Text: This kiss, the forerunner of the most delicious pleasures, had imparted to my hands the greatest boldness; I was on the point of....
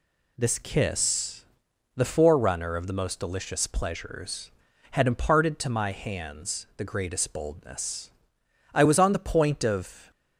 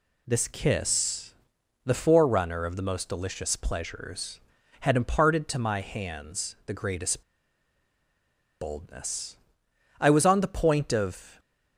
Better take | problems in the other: first | pauses between "greatest" and "boldness"; strong; at 7.2 s; 1.3 s long

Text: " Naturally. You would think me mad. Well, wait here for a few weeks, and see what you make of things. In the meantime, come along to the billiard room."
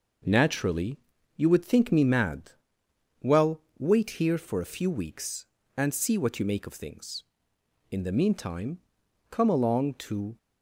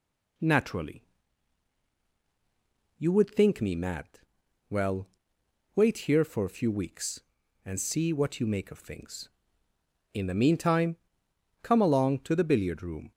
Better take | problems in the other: second | stops before "the billiard room"; at 10.3 s

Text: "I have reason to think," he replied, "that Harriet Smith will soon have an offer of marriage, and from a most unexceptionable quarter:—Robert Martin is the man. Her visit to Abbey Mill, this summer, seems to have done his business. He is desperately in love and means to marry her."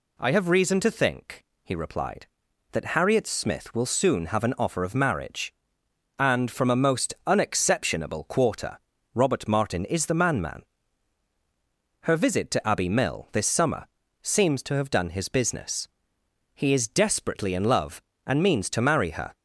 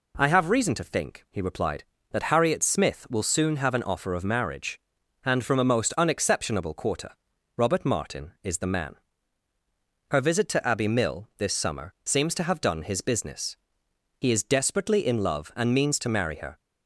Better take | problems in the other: second | says "man" twice; at 10.4 s

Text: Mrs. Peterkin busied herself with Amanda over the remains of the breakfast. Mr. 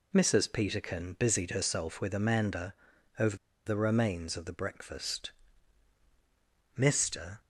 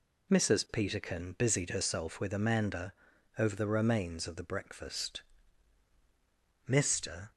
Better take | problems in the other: second | pauses between "Amanda" and "over"; noticeable; at 2.7 s; 0.46 s long; noticeable in the second // pauses between "over" and "the"; slight; at 3.3 s; 0.30 s long

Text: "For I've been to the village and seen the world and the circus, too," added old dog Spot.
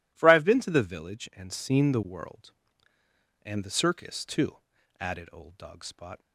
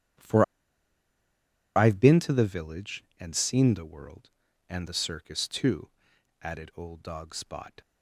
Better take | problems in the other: first | starts louder than the rest; strong; until 2.5 s; 11 dB // pauses between "For" and "I've"; strong; at 0.4 s; 1.3 s long

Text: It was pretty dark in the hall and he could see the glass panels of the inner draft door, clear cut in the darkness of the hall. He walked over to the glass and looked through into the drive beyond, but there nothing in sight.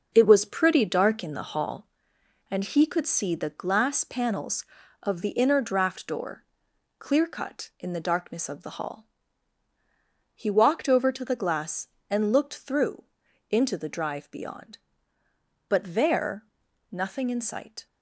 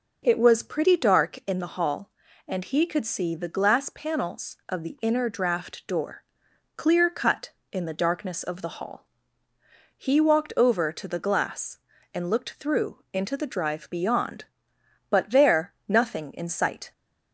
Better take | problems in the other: second | gets quieter; throughout; 6.5 dB // pauses between "through" and "into"; noticeable; at 13.0 s; 0.46 s long // pauses between "there" and "nothing"; noticeable; at 16.4 s; 0.46 s long

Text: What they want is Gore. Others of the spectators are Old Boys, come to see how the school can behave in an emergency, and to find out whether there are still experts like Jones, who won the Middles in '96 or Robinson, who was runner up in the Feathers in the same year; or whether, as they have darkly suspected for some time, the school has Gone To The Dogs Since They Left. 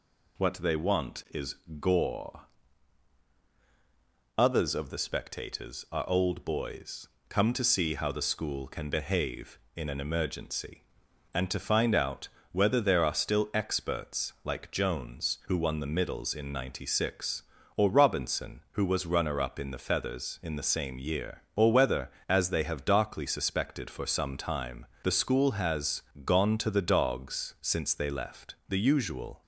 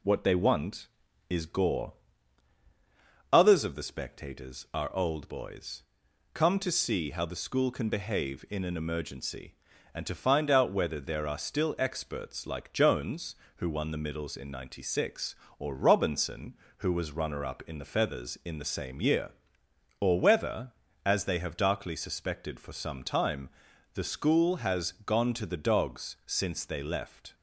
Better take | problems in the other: second | pauses between "is" and "Gore"; slight; at 1.5 s; 0.24 s long // pauses between "out" and "whether"; slight; at 12.2 s; 0.24 s long // pauses between "has" and "Gone"; slight; at 26.0 s; 0.22 s long // goes on to say "The usual"; noticeable; from 28.6 s on; 0.74 s long

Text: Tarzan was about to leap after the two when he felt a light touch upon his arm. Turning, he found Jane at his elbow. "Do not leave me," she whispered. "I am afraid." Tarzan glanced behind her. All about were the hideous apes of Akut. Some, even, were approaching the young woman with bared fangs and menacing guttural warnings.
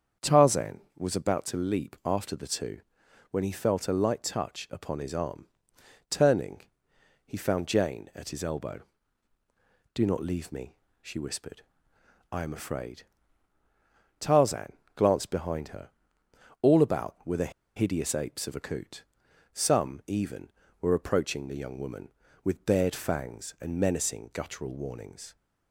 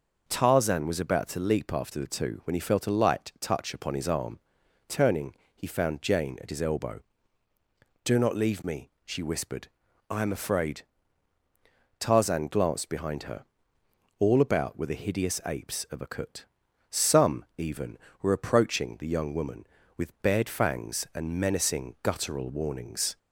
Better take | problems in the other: second | starts louder than the rest; strong; until 1.3 s; 7.5 dB // pauses between "two" and "when"; noticeable; at 2.7 s; 0.52 s long // pauses between "Tarzan" and "glanced"; slight; at 14.7 s; 0.24 s long // pauses between "the" and "hideous"; slight; at 17.5 s; 0.25 s long

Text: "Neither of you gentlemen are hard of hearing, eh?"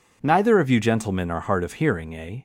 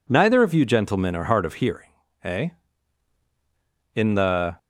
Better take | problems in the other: first | goes on to say "In the"; noticeable; from 3.9 s on; 0.64 s long

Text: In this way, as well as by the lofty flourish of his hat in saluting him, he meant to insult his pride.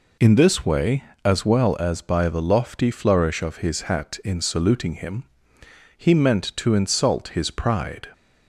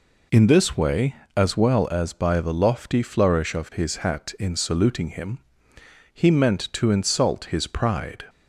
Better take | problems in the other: neither | none

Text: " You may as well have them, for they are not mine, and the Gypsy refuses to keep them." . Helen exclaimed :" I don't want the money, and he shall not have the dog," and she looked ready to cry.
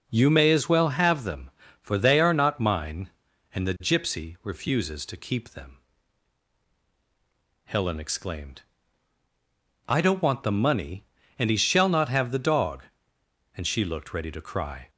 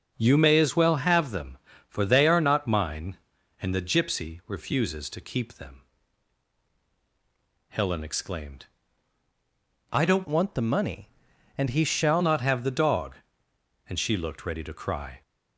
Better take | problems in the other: first | starts louder than the rest; strong; until 1.1 s; 7.5 dB; also in the first // changes voice from "want" to "shall"; from 10.2 to 12.2 s; 2.0 s long

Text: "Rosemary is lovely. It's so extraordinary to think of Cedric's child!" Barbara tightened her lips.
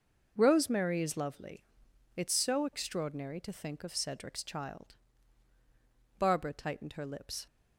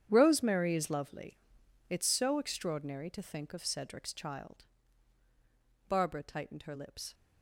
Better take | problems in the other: first | gets quieter; strong; throughout; 15 dB

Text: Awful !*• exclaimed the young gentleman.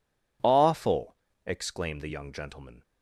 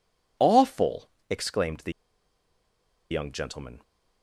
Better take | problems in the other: first | pauses between "the" and "young"; at 1.9 s; 1.1 s long

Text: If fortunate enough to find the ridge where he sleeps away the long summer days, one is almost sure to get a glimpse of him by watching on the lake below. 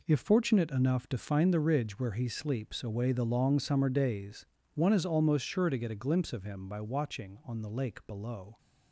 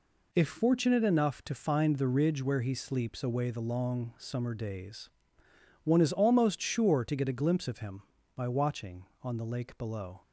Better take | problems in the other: neither | none

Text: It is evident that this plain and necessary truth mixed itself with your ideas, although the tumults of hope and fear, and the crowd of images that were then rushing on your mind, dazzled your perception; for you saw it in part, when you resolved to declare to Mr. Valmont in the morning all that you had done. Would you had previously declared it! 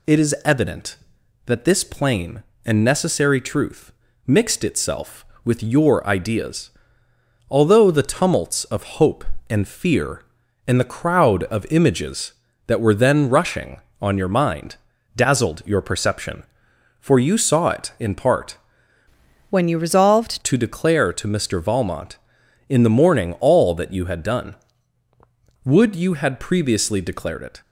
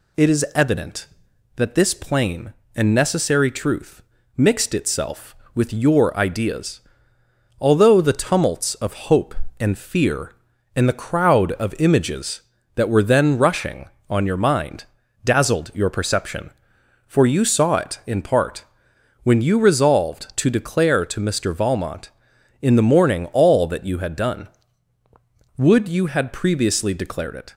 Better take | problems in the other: second | pauses between "truth" and "mixed"; slight; at 3.9 s; 0.34 s long; slight in the second // changes voice from "when" to "resolved"; from 19.4 to 20.3 s; 0.9 s long

